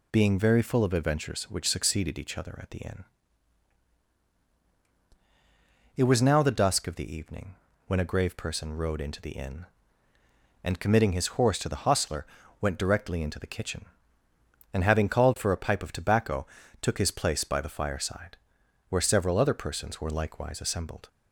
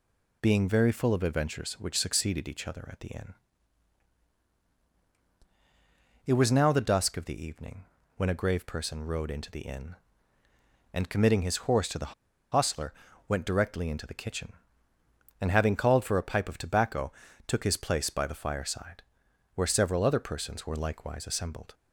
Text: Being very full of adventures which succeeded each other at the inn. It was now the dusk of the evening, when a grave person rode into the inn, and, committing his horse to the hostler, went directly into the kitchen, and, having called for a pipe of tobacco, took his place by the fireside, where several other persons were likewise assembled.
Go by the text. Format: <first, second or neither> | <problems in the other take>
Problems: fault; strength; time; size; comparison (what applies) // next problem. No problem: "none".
first | pauses between "the" and "hostler"; at 12.1 s; 0.39 s long